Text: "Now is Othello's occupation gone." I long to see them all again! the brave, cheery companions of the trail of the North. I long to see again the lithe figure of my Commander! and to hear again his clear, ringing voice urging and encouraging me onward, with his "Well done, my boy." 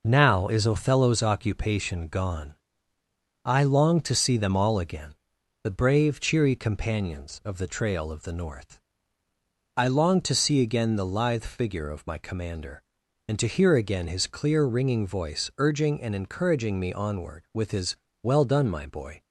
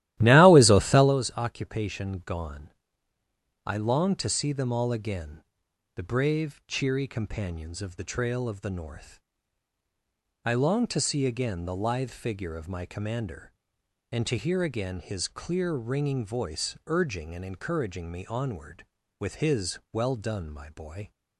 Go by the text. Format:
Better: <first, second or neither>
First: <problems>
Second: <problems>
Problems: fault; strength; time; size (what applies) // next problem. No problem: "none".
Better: first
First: pauses between "his" and "Well"; slight; at 17.9 s; 0.26 s long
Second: starts louder than the rest; strong; until 1.2 s; 14.5 dB // pauses between "his" and "Well"; slight; at 19.7 s; 0.16 s long